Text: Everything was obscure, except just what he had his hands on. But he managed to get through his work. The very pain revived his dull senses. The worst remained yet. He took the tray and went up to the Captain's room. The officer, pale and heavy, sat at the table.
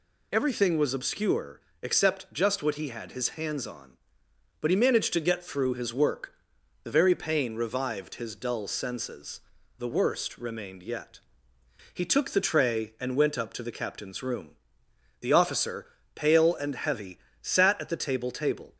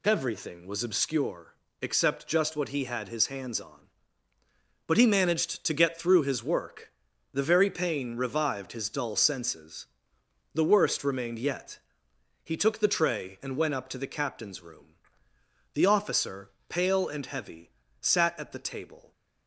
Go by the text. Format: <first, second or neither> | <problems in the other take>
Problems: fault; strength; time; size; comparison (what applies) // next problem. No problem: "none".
second | says "table" twice; at 18.3 s